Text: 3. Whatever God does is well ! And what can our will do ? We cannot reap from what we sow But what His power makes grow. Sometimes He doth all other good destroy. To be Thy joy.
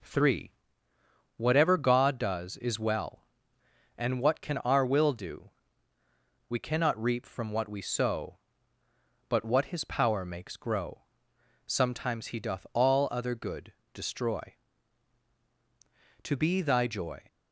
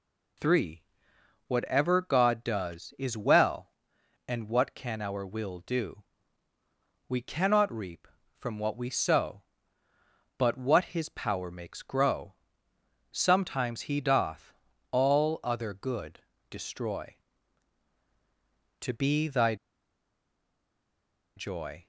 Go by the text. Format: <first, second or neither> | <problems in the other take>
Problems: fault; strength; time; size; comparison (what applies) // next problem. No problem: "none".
first | pauses between "doth" and "all"; at 14.5 s; 0.38 s long // pauses between "good" and "destroy"; slight; at 16.1 s; 0.30 s long; slight in the first // pauses between "Thy" and "joy"; strong; at 19.5 s; 1.8 s long